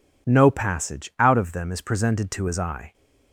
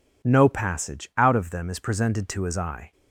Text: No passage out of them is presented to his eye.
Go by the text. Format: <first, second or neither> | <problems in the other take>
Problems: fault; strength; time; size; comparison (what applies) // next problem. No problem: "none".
neither | none